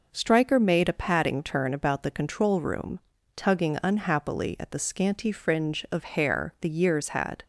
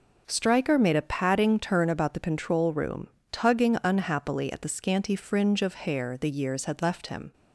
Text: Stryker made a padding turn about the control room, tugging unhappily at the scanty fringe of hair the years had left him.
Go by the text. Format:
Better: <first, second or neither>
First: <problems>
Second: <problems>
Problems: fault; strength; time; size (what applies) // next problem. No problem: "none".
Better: second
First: stops before "left him"; at 7.4 s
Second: none